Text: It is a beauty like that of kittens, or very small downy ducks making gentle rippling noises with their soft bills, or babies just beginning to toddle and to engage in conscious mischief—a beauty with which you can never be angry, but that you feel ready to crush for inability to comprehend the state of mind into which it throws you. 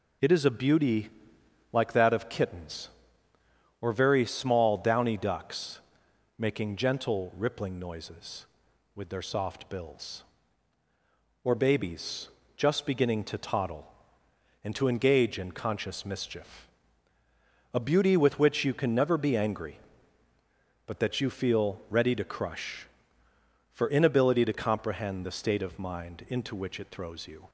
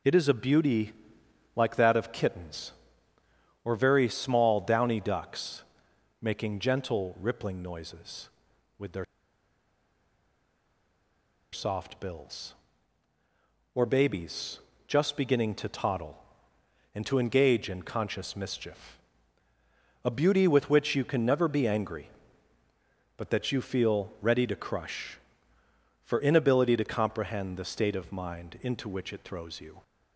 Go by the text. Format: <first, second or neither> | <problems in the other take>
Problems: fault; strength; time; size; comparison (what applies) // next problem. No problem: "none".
first | pauses between "beauty" and "like"; noticeable; at 0.9 s; 0.64 s long; noticeable in the first // pauses between "ducks" and "making"; noticeable; at 5.6 s; 0.58 s long; noticeable in the first // pauses between "their" and "soft"; strong; at 9.0 s; 2.4 s long // pauses between "babies" and "just"; slight; at 14.5 s; 0.30 s long; slight in the first